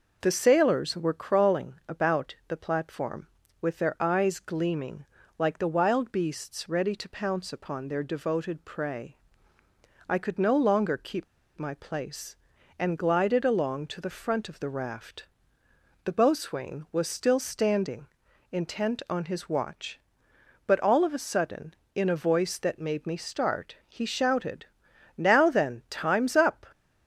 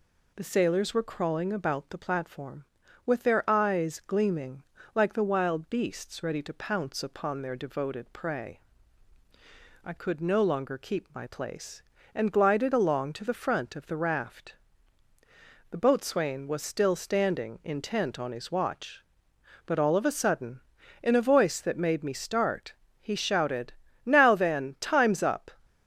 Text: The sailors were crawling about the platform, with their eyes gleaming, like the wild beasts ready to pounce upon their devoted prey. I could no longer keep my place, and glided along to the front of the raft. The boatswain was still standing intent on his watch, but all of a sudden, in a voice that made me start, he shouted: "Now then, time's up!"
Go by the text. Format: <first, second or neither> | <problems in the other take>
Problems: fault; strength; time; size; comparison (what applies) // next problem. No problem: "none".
second | pauses between "keep" and "my"; slight; at 11.2 s; 0.33 s long // pauses between "standing" and "intent"; at 18.0 s; 0.42 s long